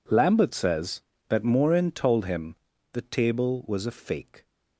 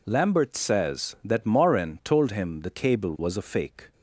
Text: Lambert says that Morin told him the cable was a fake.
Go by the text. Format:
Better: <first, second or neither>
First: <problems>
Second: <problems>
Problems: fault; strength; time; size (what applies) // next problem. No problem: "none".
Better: second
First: pauses between "him" and "the"; at 2.5 s; 0.38 s long // says "table" for "cable"; at 3.0 s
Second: none